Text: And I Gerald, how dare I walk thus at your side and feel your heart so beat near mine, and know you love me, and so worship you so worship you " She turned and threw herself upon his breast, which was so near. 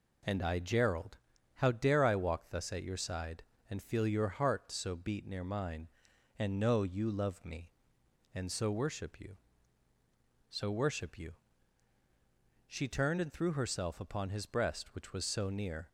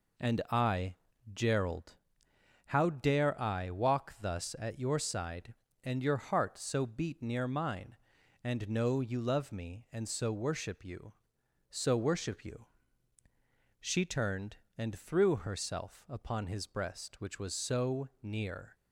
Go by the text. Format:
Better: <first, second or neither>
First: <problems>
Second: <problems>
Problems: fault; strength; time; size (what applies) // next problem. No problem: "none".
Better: first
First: none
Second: pauses between "I" and "Gerald"; at 0.9 s; 0.38 s long // skips "feel"; at 6.0 s // pauses between "so" and "near"; slight; at 18.0 s; 0.16 s long